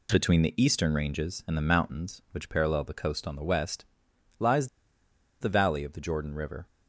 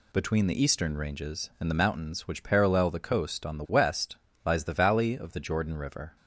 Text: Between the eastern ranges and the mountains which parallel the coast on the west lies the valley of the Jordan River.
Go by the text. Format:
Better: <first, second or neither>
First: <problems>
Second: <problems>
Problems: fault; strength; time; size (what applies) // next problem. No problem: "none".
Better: second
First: pauses between "west" and "lies"; noticeable; at 3.8 s; 0.56 s long // pauses between "lies" and "the"; noticeable; at 4.6 s; 0.74 s long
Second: pauses between "west" and "lies"; slight; at 4.1 s; 0.28 s long